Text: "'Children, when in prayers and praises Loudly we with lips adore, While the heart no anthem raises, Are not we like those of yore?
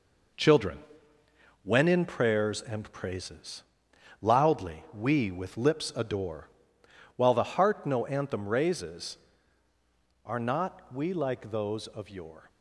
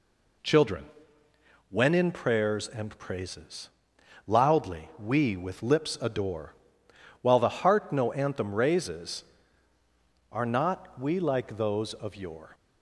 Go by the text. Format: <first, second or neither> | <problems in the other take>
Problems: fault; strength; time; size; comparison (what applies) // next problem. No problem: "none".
second | gets quieter; noticeable; throughout; 6 dB // pauses between "praises" and "Loudly"; noticeable; at 3.6 s; 0.62 s long; noticeable in the second